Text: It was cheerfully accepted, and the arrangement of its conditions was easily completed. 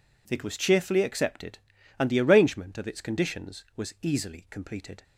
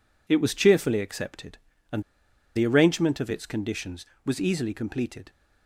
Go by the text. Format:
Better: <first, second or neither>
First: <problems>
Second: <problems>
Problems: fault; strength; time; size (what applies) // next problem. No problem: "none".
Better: first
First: none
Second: pauses between "and" and "the"; noticeable; at 2.0 s; 0.53 s long